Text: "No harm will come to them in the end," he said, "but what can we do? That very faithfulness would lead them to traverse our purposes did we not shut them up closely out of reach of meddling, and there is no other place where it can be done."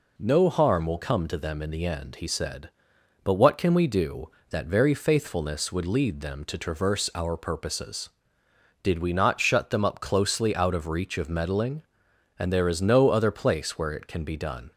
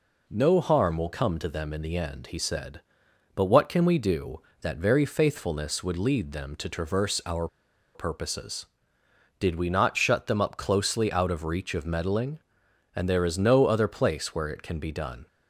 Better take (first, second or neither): first